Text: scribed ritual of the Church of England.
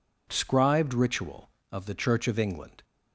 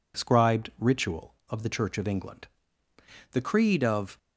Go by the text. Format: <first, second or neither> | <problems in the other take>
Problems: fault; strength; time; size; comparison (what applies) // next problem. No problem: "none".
first | goes on to say "The Creed of"; noticeable; from 3.3 s on; 0.86 s long